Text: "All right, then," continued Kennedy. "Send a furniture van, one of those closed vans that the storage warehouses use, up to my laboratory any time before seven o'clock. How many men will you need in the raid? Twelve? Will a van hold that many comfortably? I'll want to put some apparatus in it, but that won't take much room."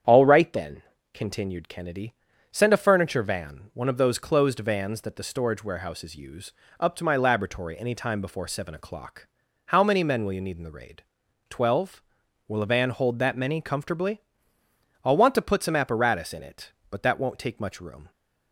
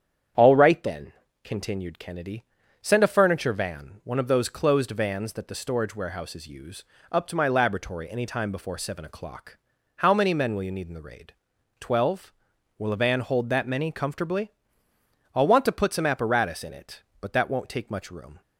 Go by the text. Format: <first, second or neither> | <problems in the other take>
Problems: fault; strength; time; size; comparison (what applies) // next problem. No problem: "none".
neither | starts louder than the rest; strong; the same in both